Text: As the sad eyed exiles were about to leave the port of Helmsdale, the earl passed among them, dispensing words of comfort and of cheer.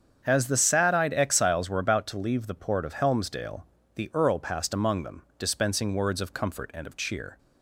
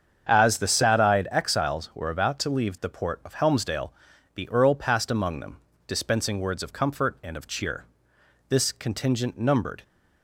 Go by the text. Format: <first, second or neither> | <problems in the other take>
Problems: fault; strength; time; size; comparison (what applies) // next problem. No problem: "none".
first | starts louder than the rest; strong; until 1.3 s; 8 dB; strong in the first // goes on to say "This contingent numbered"; from 8.4 s on; 1.3 s long